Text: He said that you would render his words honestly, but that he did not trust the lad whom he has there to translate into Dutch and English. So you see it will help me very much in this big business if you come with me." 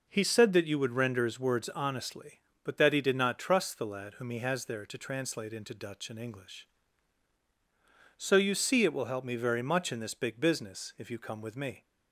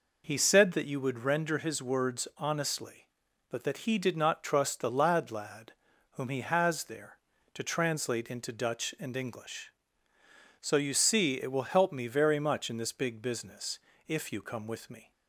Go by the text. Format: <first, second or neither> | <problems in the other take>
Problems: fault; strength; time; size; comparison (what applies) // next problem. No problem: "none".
first | says "lad" twice; at 5.2 s // pauses between "business" and "if"; slight; at 13.7 s; 0.30 s long